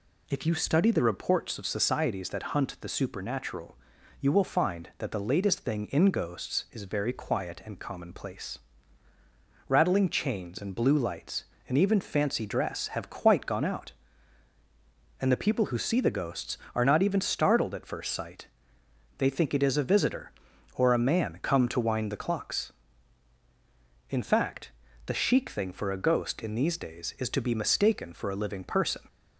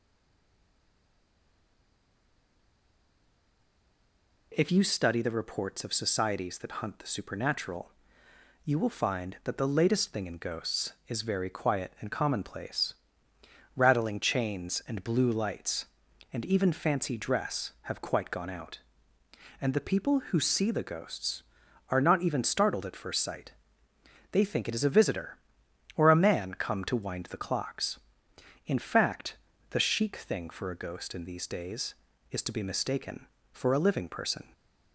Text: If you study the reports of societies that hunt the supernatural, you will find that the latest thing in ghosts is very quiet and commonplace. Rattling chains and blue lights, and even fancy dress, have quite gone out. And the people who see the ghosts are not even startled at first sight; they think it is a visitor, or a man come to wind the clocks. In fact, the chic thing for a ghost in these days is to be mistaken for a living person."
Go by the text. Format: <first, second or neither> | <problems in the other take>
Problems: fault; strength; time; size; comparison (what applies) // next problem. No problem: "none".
first | stays silent before the first word; strong; until 4.5 s; 4.5 s long